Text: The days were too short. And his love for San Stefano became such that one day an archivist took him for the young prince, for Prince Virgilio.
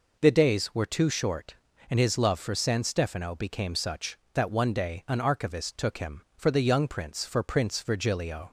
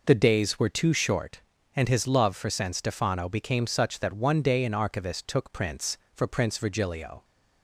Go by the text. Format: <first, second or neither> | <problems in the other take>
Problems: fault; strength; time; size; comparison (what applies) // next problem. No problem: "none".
first | skips "him for the young"; at 5.5 s